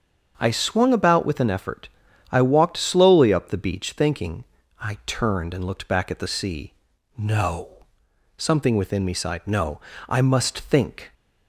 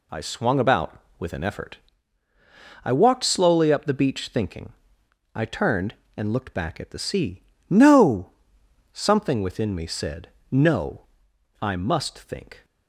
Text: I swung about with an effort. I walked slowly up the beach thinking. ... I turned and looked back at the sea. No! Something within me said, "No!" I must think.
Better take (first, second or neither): second